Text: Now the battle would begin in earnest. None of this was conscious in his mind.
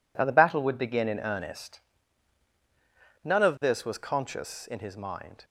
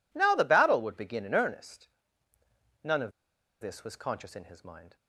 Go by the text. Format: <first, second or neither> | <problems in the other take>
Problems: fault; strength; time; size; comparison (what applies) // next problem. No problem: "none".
first | pauses between "of" and "this"; noticeable; at 3.1 s; 0.49 s long